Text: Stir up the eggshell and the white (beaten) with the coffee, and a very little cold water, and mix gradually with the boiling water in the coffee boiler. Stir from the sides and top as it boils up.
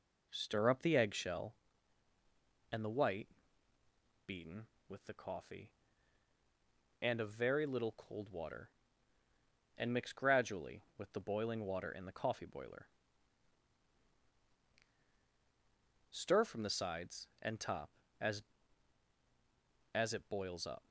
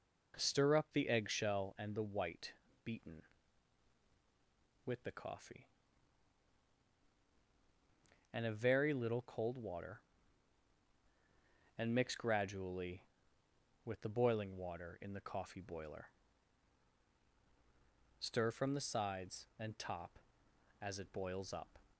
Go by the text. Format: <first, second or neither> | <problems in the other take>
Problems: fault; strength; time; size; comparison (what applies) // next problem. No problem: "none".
second | says "as" twice; at 19.9 s